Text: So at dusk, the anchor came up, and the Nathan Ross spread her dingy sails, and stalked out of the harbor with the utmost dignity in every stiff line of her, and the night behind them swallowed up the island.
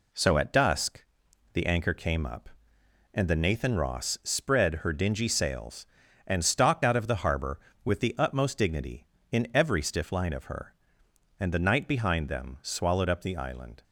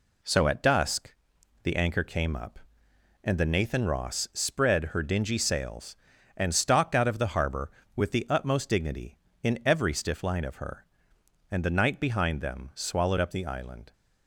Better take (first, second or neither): neither